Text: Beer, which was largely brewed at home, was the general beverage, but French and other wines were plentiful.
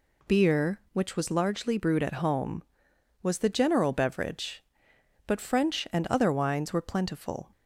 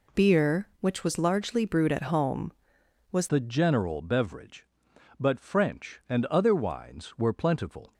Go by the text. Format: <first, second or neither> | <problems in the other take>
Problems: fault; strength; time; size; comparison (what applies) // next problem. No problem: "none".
first | changes voice at "the"; from 3.2 s on; 4.7 s long